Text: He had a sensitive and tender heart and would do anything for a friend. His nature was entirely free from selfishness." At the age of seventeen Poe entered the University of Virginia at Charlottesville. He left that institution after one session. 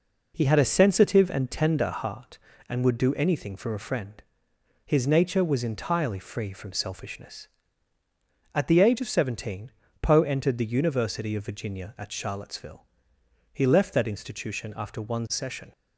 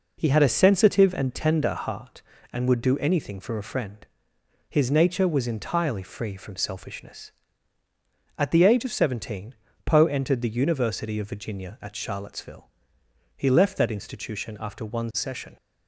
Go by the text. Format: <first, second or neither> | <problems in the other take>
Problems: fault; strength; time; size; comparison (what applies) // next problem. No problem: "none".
neither | pauses between "seventeen" and "Poe"; slight; the same in both